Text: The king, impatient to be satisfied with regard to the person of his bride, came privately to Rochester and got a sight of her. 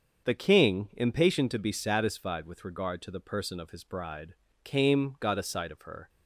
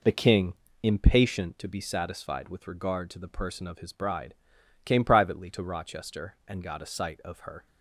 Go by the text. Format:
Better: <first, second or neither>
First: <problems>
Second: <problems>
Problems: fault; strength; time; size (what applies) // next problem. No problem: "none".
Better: second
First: starts louder than the rest; until 1.3 s; 6.5 dB // skips "privately to Rochester and"; at 5.1 s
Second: none